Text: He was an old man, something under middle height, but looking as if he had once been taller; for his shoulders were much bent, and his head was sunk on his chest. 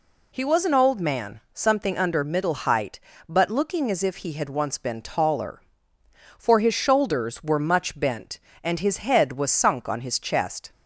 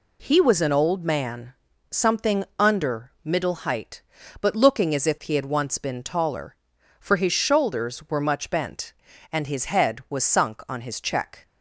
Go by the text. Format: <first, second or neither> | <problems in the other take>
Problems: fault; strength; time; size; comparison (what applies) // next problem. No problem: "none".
first | says "check" for "chest"; at 11.0 s